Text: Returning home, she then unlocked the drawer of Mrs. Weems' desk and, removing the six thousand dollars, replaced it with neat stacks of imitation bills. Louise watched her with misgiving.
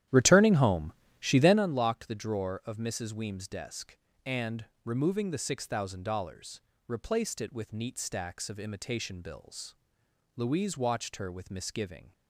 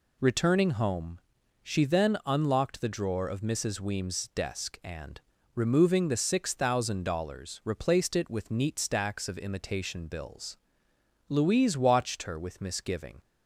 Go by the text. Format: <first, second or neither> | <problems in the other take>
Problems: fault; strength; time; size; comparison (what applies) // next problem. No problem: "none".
second | starts louder than the rest; strong; until 1.6 s; 12 dB